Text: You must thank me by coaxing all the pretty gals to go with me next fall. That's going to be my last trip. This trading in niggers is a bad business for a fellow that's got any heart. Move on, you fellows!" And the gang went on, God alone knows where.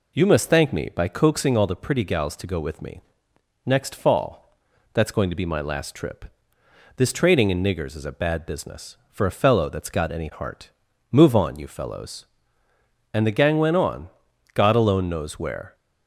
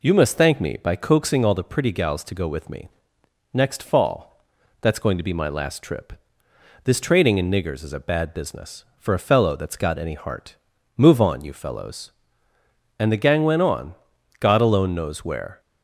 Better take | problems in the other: neither | pauses between "me" and "next"; noticeable; the same in both

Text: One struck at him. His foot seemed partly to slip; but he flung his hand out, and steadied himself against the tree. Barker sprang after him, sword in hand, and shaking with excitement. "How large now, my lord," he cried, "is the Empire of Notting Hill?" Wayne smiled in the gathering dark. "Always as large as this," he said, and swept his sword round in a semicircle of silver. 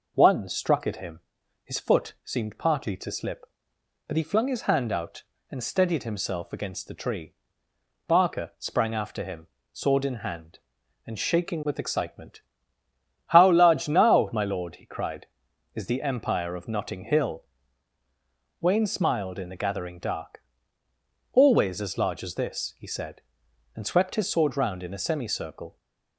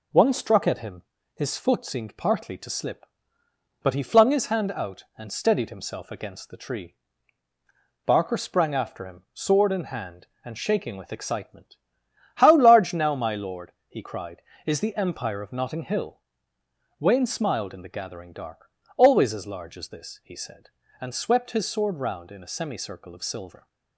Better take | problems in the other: second | stops before "of silver"; at 25.7 s

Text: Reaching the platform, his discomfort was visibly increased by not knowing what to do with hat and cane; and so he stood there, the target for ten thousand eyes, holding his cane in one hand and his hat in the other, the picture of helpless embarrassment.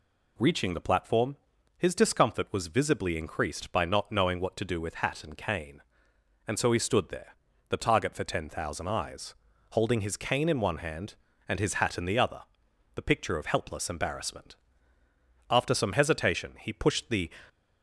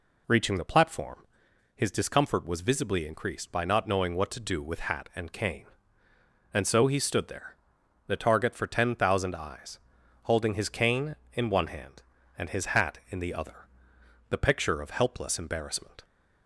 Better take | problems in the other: second | goes on to say "After some hesitation he pushed the"; strong; from 15.4 s on; 1.8 s long

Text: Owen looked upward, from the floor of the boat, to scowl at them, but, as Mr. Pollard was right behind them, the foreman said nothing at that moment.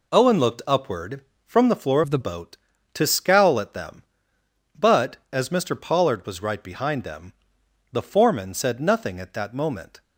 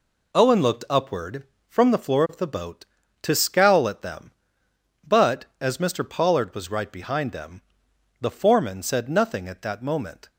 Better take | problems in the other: second | changes voice from "of" to "the"; from 2.0 to 2.1 s; 0.1 s long

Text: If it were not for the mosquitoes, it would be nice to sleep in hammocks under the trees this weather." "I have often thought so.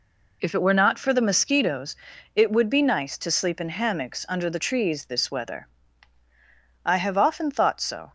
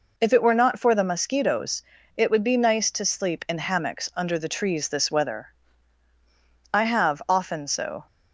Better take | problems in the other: first | skips "thought"; at 7.6 s

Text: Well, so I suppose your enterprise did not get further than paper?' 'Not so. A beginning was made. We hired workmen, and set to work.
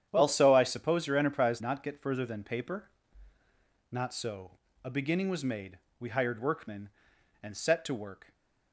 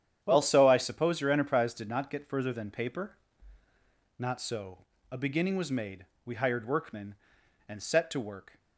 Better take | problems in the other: second | starts louder than the rest; strong; until 1.1 s; 9.5 dB; strong in the second // skips "did"; at 1.6 s

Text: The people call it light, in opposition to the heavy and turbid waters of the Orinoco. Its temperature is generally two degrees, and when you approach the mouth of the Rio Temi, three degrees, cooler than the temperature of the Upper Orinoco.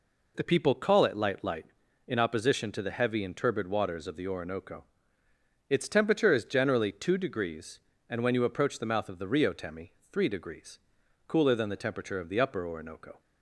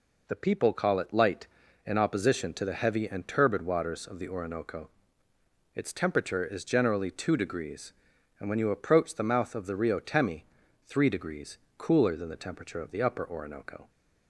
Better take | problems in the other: second | says "light" twice; at 1.4 s

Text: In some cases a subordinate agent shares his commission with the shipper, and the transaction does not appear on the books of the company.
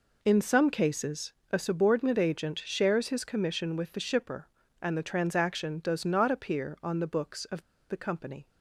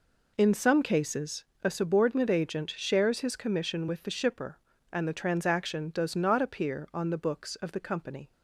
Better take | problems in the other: second | pauses between "cases" and "a"; slight; at 1.3 s; 0.18 s long; slight in the second // pauses between "of" and "the"; slight; at 7.6 s; 0.29 s long

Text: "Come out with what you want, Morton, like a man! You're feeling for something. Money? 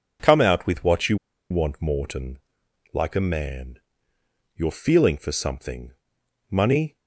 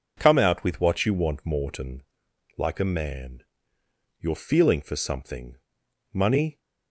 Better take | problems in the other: second | pauses between "you" and "want"; slight; at 1.1 s; 0.33 s long

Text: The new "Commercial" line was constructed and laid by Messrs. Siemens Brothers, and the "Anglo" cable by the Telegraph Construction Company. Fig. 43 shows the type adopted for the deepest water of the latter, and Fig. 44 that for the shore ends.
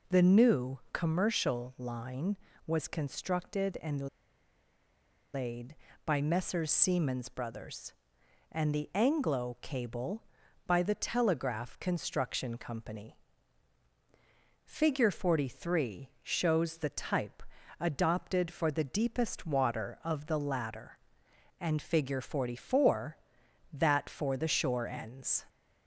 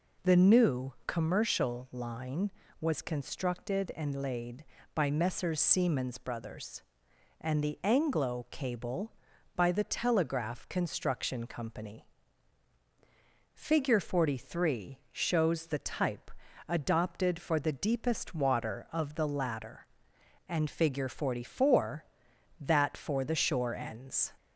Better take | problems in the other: second | pauses between "new" and "Commercial"; slight; at 0.7 s; 0.16 s long; slight in the second // pauses between "and" and "laid"; strong; at 4.0 s; 1.2 s long // pauses between "type" and "adopted"; slight; at 17.4 s; 0.34 s long; slight in the second

